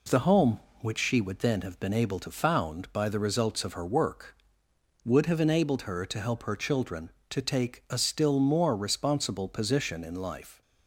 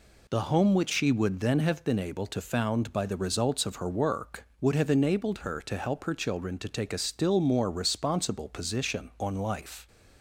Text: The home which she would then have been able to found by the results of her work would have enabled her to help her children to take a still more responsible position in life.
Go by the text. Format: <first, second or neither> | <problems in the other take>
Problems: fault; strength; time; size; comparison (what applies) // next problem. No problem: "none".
first | says "on" for "in"; at 9.2 s